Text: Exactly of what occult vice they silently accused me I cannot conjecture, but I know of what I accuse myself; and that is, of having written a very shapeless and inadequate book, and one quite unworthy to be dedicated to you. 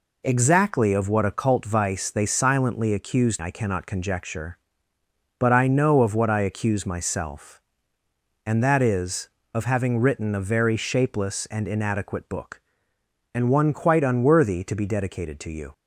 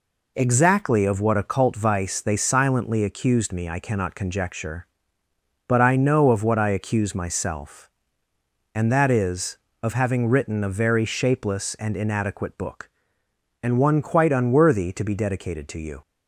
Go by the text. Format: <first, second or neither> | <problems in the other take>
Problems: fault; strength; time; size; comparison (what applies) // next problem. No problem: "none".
second | skips "me"; at 3.4 s